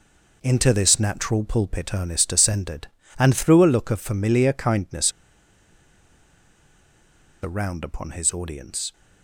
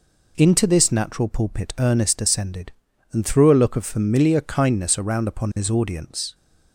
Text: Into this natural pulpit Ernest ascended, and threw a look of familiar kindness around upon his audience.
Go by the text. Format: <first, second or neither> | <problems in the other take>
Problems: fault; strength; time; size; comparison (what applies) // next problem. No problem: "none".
second | pauses between "kindness" and "around"; strong; at 5.1 s; 2.3 s long